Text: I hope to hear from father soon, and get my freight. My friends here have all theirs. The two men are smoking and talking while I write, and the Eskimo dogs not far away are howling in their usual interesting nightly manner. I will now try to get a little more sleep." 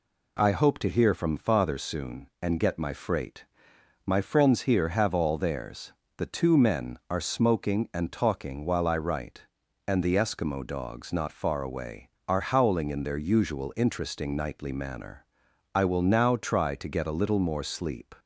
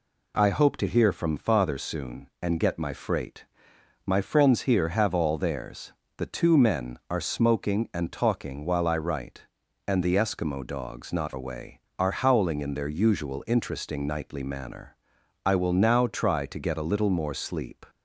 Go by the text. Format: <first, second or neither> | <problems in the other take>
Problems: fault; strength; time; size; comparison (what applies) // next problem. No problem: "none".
first | skips "far"; at 11.3 s